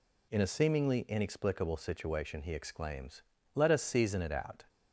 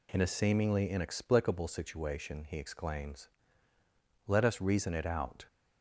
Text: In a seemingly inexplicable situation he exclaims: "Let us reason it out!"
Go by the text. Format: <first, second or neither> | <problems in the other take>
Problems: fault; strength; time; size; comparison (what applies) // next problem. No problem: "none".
second | says "season" for "reason"; at 3.8 s